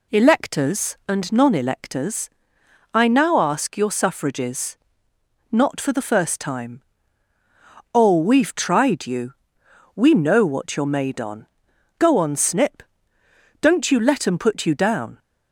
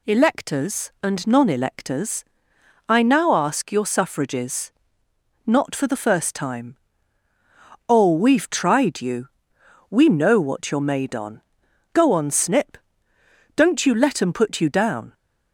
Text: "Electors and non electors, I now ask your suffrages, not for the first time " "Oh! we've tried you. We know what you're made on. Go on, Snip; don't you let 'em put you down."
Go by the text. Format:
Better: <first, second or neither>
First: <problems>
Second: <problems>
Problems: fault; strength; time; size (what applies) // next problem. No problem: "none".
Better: second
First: starts louder than the rest; slight; until 1.1 s; 2 dB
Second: none